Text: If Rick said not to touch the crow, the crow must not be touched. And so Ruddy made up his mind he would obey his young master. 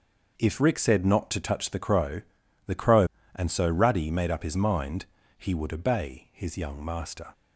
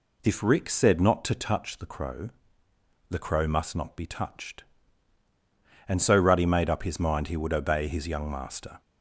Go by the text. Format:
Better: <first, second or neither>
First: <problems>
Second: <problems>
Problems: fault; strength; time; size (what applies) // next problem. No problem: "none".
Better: second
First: skips "must not be touched"; at 3.2 s // pauses between "mind" and "he"; slight; at 5.0 s; 0.32 s long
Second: none